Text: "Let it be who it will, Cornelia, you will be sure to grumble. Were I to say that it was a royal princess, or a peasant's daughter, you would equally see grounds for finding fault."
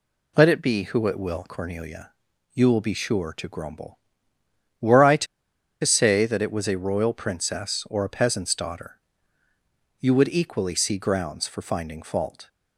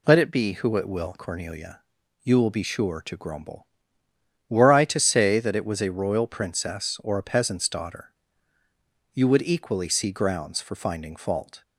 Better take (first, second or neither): second